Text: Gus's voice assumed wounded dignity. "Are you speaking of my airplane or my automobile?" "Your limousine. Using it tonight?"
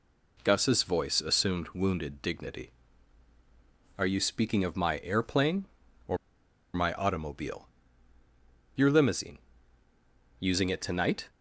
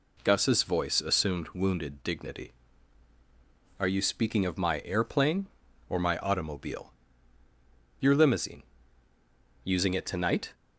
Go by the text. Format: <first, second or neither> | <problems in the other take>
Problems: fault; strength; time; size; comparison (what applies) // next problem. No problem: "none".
second | pauses between "or" and "my"; noticeable; at 6.1 s; 0.57 s long